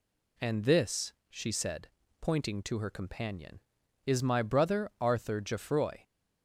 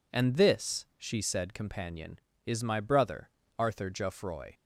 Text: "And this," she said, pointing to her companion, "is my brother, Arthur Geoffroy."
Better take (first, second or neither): first